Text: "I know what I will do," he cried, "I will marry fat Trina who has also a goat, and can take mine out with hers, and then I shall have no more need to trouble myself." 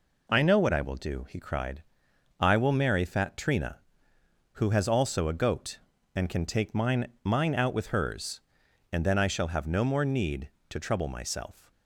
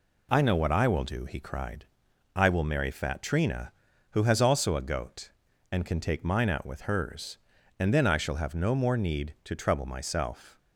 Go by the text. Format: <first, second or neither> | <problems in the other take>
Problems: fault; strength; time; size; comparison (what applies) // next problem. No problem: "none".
second | says "mine" twice; at 7.2 s